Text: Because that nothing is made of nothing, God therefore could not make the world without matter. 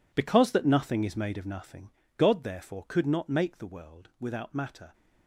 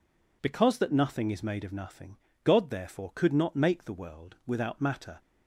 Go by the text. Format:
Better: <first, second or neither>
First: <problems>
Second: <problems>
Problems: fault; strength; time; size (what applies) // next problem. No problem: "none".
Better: second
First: gets quieter; strong; throughout; 14 dB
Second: none